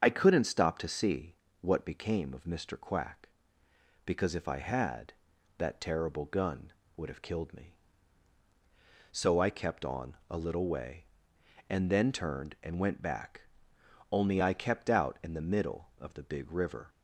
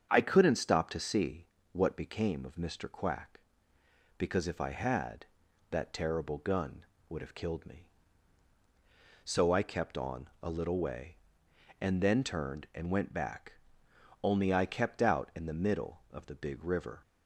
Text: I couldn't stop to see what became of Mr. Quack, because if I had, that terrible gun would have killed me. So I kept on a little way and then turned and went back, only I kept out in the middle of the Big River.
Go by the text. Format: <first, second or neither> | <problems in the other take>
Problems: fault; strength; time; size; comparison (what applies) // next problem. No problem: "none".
second | loses the start of "I"; at 0.0 s; 35 ms // starts louder than the rest; strong; until 1.0 s; 7.5 dB; strong in the second // pauses between "see" and "what"; slight; at 1.3 s; 0.28 s long; slight in the second